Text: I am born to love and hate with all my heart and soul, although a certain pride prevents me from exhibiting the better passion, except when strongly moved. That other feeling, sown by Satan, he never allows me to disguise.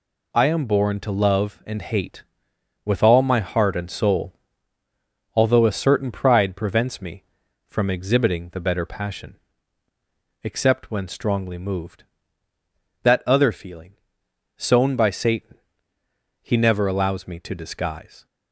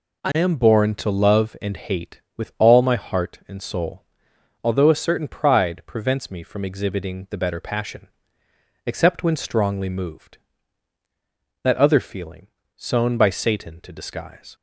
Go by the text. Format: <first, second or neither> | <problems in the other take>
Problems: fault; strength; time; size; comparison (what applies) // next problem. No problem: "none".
first | skips "he never allows me"; at 13.8 s